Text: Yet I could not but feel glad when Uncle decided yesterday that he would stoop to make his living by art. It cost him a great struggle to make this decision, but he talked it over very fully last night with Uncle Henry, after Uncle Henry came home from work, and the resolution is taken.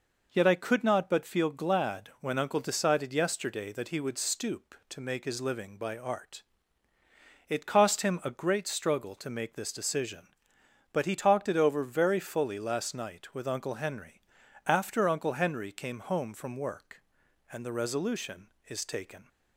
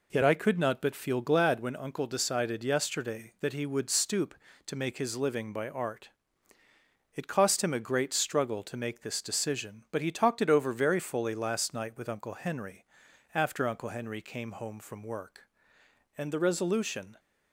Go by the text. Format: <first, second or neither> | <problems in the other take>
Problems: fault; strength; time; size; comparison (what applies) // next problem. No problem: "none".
first | stops before "is taken"; at 17.1 s